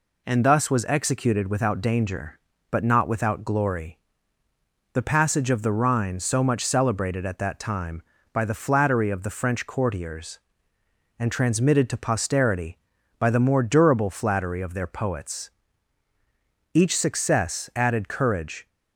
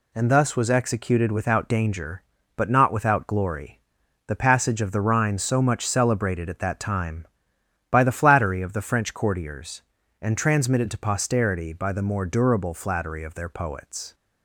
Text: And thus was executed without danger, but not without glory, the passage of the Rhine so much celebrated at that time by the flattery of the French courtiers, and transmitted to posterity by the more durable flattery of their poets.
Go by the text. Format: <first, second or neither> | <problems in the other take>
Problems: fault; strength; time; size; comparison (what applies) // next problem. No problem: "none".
second | goes on to say "Each success added courage"; strong; from 16.7 s on; 1.9 s long